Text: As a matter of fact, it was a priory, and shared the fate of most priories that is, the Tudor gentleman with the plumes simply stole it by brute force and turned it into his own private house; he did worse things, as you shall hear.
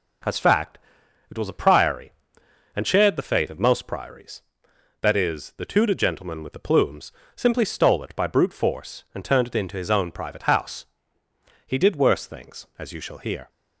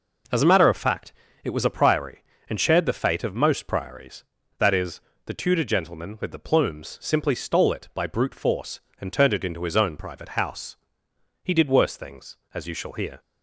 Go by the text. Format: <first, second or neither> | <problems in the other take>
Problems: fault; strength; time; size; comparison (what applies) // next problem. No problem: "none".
second | skips "a matter of"; at 0.3 s // pauses between "plumes" and "simply"; slight; at 7.1 s; 0.24 s long